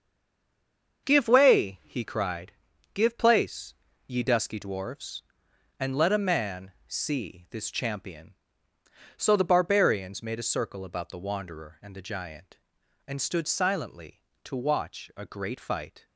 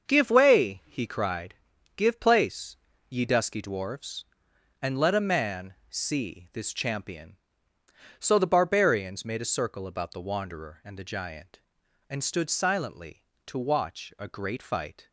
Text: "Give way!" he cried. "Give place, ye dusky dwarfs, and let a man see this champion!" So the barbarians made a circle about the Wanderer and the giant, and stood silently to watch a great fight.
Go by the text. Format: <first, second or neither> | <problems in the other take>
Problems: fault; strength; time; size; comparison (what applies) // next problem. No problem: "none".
second | stays silent before the first word; until 1.0 s; 1.0 s long // starts louder than the rest; until 2.1 s; 6.5 dB; also in the second // pauses between "man" and "see"; slight; at 6.7 s; 0.16 s long; slight in the second